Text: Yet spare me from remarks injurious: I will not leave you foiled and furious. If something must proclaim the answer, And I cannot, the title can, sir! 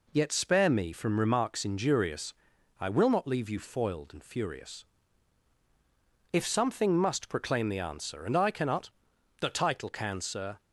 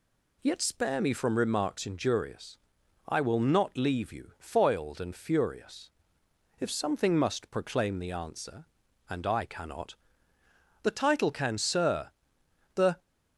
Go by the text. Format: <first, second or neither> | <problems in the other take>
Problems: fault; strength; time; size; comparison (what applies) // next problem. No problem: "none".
first | goes on to say "The"; slight; from 12.7 s on; 0.24 s long